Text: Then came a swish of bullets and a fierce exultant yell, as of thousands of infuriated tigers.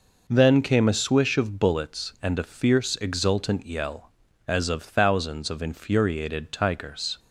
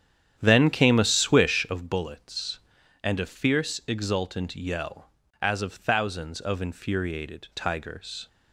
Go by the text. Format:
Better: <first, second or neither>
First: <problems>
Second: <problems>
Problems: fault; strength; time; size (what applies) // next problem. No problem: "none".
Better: first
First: none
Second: starts louder than the rest; strong; until 1.8 s; 9.5 dB